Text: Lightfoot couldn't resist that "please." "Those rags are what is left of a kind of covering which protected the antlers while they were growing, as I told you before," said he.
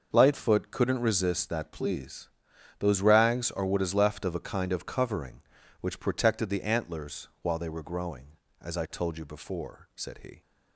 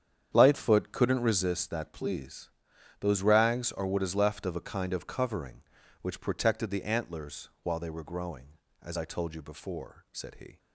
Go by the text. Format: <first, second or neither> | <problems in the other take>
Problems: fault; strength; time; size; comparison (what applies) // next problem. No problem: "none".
first | starts louder than the rest; strong; until 1.5 s; 8.5 dB // pauses between "antlers" and "while"; slight; at 7.4 s; 0.16 s long; slight in the first